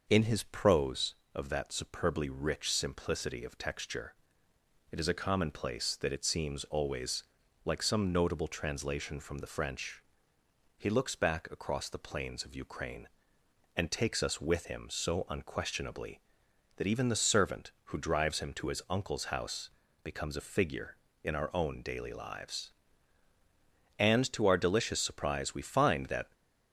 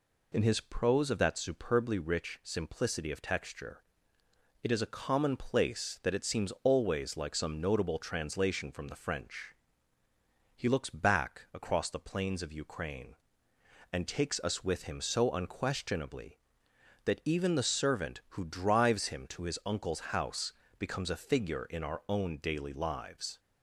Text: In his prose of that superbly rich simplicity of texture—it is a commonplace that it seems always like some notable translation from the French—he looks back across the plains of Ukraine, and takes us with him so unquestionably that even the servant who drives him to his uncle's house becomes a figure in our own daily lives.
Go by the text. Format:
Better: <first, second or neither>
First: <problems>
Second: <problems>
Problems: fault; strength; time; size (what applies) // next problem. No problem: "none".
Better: second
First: pauses between "always" and "like"; at 7.2 s; 0.40 s long // pauses between "house" and "becomes"; slight; at 19.6 s; 0.32 s long // goes on to say "And to our delicious surprise we find that"; strong; from 23.9 s on; 2.3 s long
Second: pauses between "house" and "becomes"; slight; at 20.5 s; 0.24 s long